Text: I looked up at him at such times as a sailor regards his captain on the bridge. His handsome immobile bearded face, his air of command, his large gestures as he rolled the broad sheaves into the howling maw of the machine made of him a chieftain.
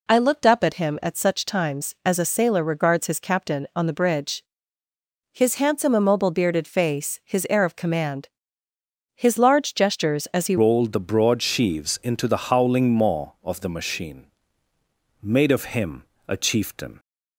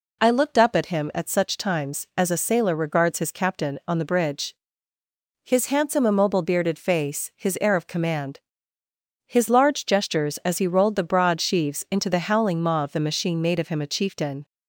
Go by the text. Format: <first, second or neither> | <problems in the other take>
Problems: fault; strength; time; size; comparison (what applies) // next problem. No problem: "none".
second | changes voice at "rolled"; from 10.5 s on; 6.4 s long // pauses between "machine" and "made"; noticeable; at 14.2 s; 0.96 s long // pauses between "him" and "a"; slight; at 16.0 s; 0.24 s long